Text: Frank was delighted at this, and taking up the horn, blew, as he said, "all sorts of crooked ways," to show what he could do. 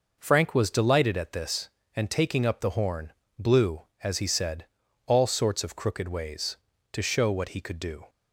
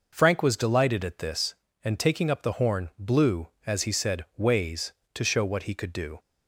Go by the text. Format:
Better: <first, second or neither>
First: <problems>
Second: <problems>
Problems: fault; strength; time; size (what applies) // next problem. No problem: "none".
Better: first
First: none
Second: skips "all sorts of crooked"; at 4.3 s